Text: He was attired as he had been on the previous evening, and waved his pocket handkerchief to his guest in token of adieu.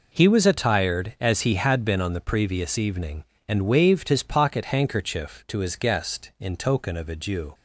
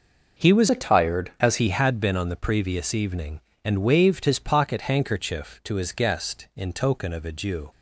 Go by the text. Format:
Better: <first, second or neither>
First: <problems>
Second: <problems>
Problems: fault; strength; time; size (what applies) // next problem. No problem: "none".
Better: first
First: none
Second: changes voice from "attired" to "as"; from 0.6 to 1.5 s; 0.9 s long